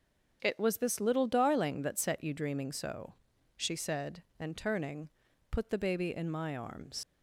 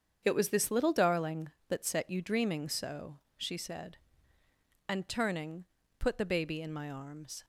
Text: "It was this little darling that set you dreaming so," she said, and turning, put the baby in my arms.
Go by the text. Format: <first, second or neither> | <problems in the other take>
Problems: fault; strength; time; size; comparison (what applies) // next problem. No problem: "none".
second | starts louder than the rest; until 1.4 s; 6.5 dB; strong in the second // leaves "arms" unfinished; at 7.0 s; 90 ms